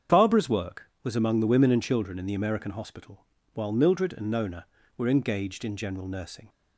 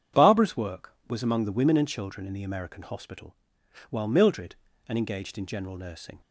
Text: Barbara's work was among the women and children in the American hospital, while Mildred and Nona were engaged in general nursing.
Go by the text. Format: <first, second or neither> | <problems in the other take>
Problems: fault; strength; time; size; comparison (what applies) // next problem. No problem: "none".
first | starts louder than the rest; strong; until 1.3 s; 8.5 dB; strong in the first // skips "Nona were"; at 4.9 s